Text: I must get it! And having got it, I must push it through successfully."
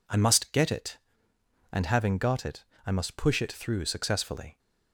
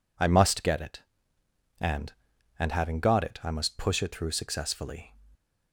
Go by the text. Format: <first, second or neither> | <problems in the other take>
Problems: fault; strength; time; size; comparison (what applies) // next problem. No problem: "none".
first | says "And" twice; at 2.5 s